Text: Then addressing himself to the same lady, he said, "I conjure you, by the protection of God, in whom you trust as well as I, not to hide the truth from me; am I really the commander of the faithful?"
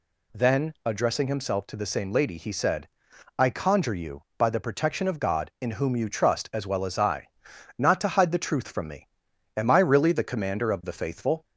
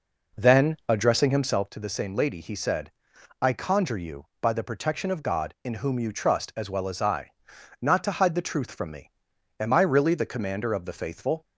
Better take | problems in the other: first | starts louder than the rest; noticeable; until 1.7 s; 4.5 dB

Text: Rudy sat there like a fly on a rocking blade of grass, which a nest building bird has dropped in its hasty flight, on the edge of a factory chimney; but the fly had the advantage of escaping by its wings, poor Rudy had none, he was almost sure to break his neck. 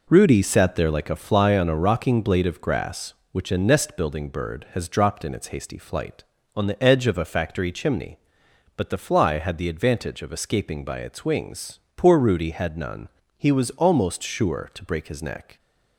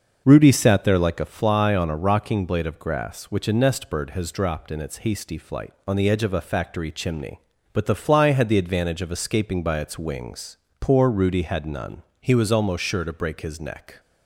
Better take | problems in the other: first | starts louder than the rest; noticeable; until 1.2 s; 6 dB // skips "building"; at 3.8 s

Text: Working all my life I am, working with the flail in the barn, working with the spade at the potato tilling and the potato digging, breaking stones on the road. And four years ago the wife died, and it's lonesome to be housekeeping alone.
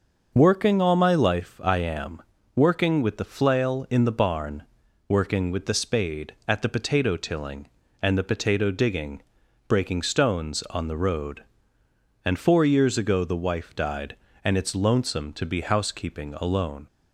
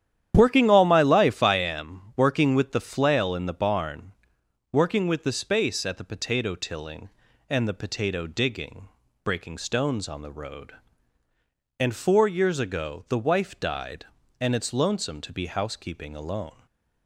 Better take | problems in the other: first | starts louder than the rest; strong; until 1.3 s; 10.5 dB; also in the first // says "space" for "spade"; at 5.3 s // stays silent after the last word; slight; from 16.5 s on; 0.5 s long

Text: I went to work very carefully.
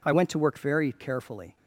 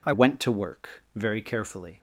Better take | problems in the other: first | changes voice at "went"; from 0.1 s on; 1.8 s long

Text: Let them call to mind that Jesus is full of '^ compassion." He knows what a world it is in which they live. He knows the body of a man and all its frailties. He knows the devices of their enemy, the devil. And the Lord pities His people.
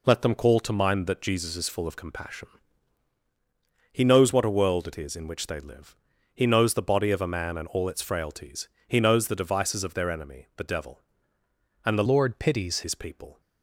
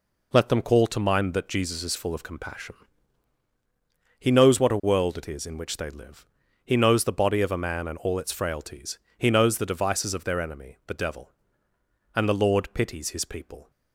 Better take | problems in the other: second | changes voice from "Lord" to "pities"; from 12.0 to 12.8 s; 0.8 s long

